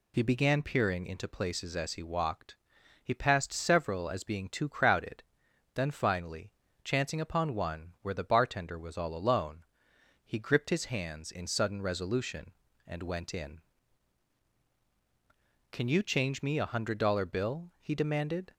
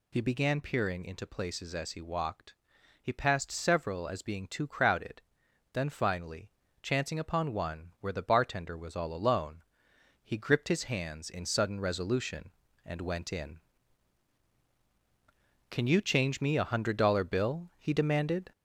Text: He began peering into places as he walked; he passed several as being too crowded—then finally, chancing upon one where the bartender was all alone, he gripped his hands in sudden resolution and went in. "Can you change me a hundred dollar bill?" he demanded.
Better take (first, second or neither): first